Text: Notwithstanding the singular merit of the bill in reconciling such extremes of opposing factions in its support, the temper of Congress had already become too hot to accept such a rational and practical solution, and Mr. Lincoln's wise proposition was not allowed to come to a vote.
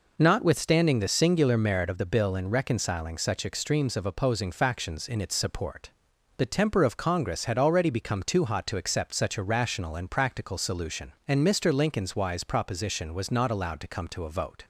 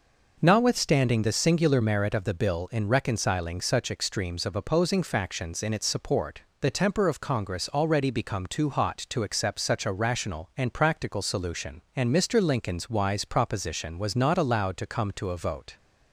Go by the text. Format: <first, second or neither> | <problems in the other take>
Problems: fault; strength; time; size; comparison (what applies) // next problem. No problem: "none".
first | skips "had"; at 7.7 s